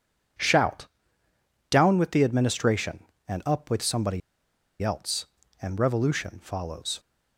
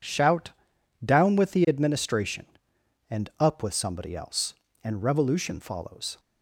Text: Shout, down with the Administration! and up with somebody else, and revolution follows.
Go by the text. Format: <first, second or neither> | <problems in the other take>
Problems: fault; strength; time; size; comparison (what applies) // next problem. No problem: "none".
second | pauses between "somebody" and "else"; noticeable; at 4.2 s; 0.62 s long